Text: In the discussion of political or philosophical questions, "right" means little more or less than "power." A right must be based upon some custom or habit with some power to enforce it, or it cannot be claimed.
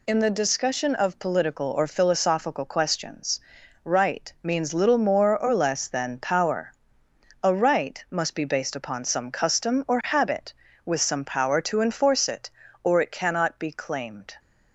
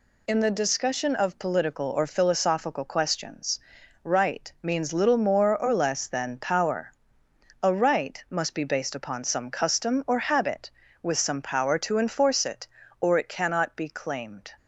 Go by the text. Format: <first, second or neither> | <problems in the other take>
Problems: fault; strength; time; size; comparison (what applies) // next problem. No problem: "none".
neither | none